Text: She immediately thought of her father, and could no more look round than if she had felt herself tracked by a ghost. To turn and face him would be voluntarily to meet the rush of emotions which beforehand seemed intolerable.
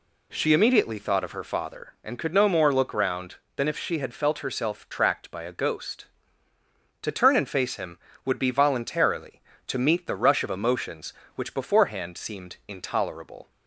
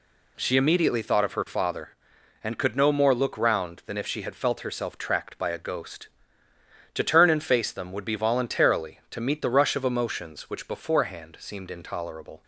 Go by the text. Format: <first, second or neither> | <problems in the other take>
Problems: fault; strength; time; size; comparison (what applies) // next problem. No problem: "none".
first | says "them" for "him"; at 7.7 s